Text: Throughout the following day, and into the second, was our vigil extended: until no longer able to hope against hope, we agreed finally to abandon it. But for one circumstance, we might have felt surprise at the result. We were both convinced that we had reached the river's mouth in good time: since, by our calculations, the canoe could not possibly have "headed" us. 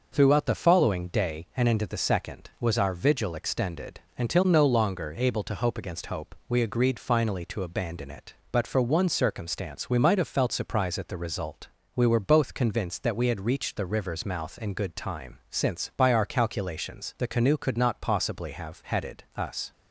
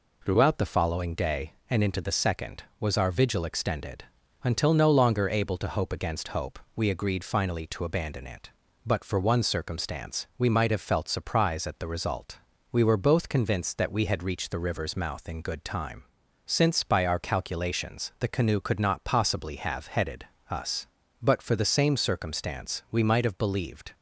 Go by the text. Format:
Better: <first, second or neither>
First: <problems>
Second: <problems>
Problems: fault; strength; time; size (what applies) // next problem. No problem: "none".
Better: first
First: none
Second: pauses between "headed" and "us"; slight; at 20.2 s; 0.24 s long // goes on to say "But for the same circumstance we might have believed"; strong; from 21.2 s on; 2.7 s long